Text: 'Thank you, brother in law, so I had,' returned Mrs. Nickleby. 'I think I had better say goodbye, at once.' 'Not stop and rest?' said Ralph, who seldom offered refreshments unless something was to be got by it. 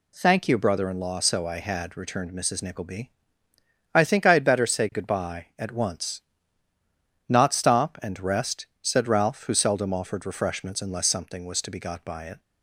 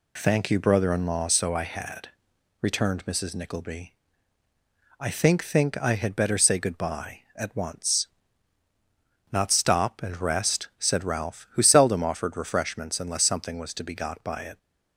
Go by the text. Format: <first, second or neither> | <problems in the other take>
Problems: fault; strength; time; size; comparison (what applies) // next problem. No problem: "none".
first | says "think" twice; at 5.4 s